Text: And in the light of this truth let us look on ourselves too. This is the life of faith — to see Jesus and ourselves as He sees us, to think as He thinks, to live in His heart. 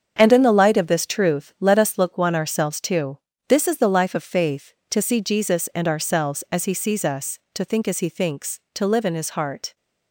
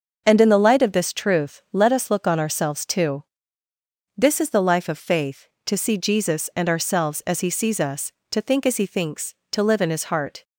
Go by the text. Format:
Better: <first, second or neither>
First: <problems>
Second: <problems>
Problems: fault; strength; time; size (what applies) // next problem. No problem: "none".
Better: second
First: starts louder than the rest; strong; until 1.1 s; 7.5 dB // says "one" for "on"; at 2.1 s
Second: starts louder than the rest; until 1.2 s; 6.5 dB